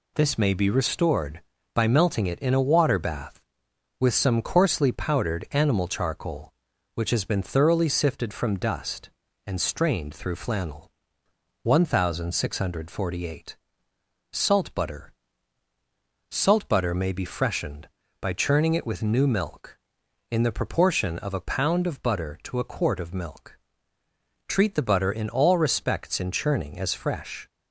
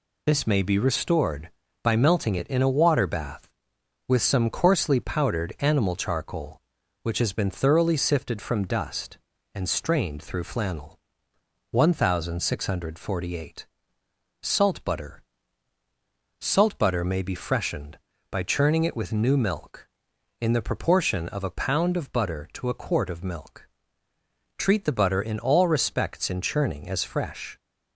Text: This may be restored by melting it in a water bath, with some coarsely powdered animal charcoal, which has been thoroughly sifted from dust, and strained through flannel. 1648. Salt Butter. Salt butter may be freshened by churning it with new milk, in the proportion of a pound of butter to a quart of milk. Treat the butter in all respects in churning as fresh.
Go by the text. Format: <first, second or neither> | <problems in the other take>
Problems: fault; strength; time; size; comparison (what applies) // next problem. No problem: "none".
first | loses the start of "This"; at 0.2 s; 25 ms